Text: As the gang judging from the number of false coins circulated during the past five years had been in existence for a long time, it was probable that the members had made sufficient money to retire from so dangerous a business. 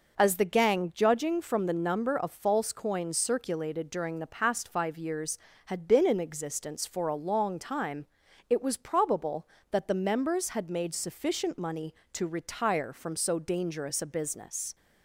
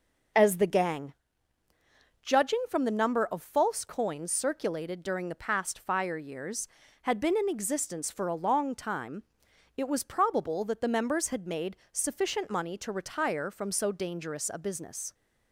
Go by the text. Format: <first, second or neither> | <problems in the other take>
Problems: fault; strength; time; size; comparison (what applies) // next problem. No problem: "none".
first | pauses between "gang" and "judging"; at 1.1 s; 1.0 s long // says "fire" for "five"; at 5.7 s // pauses between "made" and "sufficient"; slight; at 11.7 s; 0.16 s long